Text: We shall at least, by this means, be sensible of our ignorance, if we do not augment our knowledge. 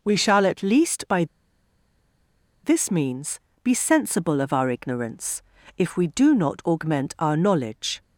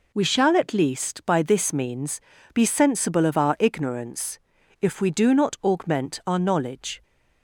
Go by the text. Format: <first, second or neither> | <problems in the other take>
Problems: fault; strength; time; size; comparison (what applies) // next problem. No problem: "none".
second | pauses between "by" and "this"; strong; at 1.2 s; 1.3 s long